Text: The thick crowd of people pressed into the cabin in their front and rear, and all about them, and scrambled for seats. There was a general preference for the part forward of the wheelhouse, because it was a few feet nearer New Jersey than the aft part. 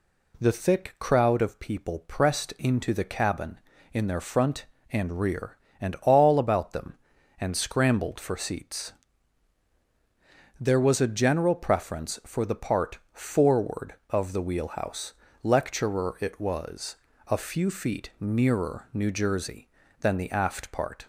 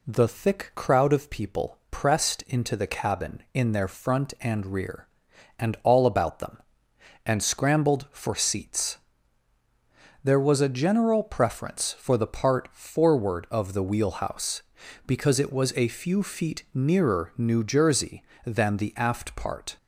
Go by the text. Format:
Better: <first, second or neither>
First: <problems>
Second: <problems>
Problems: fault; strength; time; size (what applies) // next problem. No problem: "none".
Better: second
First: says "lecturer" for "because"; at 15.4 s // pauses between "was" and "a"; slight; at 16.9 s; 0.32 s long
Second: none